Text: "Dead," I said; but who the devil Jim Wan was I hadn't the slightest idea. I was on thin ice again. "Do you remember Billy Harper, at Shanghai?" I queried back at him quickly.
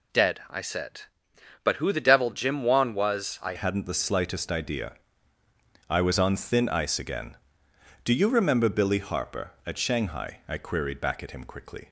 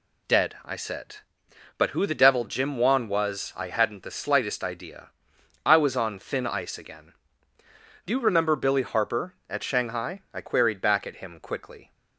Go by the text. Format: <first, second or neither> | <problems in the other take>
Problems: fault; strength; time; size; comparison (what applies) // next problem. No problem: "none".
second | changes voice at "hadn't"; from 3.5 s on; 8.3 s long